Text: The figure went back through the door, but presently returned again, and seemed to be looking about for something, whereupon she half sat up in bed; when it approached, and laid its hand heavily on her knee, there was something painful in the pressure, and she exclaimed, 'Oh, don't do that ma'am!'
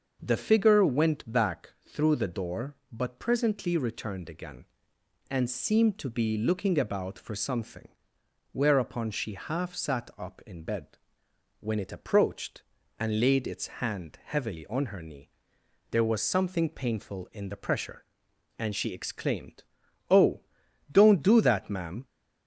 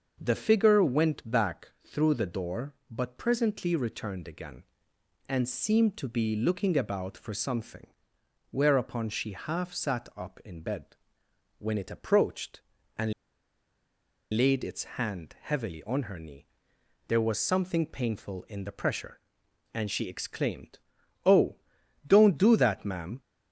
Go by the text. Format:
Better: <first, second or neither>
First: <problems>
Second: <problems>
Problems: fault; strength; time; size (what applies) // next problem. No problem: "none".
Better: first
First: starts louder than the rest; until 1.2 s; 6.5 dB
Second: starts louder than the rest; until 1.2 s; 6.5 dB // pauses between "and" and "laid"; at 13.1 s; 1.2 s long